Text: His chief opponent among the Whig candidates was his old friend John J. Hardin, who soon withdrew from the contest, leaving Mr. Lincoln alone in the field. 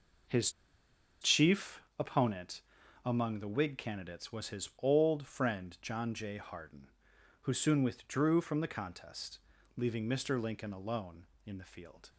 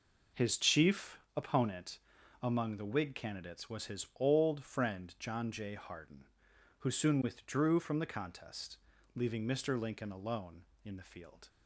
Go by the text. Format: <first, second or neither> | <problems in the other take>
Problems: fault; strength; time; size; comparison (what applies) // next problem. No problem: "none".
second | pauses between "His" and "chief"; noticeable; at 0.5 s; 0.70 s long // pauses between "chief" and "opponent"; slight; at 1.8 s; 0.16 s long; slight in the second // pauses between "opponent" and "among"; at 2.6 s; 0.44 s long; also in the second